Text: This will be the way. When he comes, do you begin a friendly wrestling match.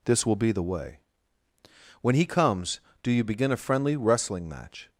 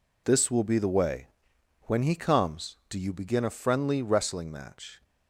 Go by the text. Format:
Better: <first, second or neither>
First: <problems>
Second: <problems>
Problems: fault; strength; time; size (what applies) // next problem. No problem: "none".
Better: neither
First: none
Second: none